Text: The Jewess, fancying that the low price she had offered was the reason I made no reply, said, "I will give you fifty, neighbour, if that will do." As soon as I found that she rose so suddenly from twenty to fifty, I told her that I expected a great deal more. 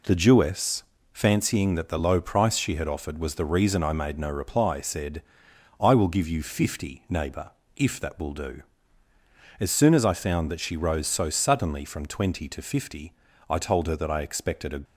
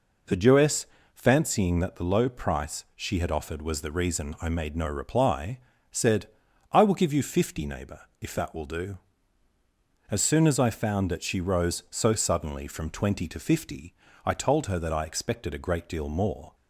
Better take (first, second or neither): second